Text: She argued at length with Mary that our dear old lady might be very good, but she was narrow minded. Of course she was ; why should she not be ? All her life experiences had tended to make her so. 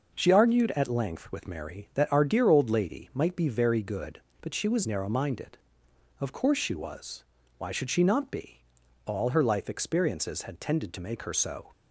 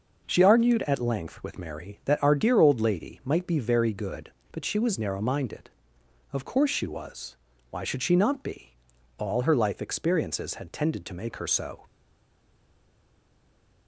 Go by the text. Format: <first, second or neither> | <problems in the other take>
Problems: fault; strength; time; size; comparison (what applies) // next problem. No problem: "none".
first | starts louder than the rest; noticeable; until 1.2 s; 6 dB; noticeable in the first // stays silent after the last word; noticeable; from 11.8 s on; 2.0 s long